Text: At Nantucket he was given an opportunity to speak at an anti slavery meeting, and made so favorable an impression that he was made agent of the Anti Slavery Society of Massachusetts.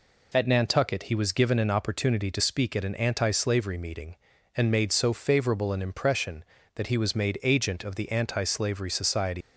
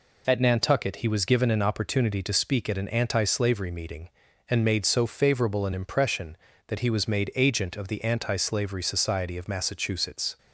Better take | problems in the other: second | stops before "of Massachusetts"; at 9.4 s

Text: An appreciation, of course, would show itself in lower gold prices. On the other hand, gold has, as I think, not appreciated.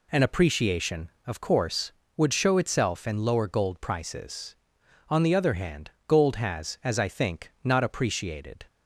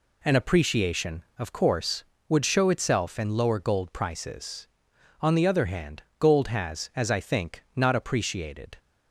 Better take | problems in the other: neither | none

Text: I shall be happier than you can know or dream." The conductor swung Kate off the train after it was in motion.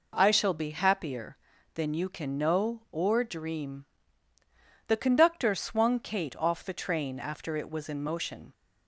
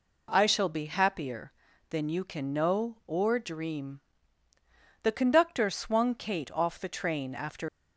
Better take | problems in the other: first | stops before "it was in motion"; at 7.6 s

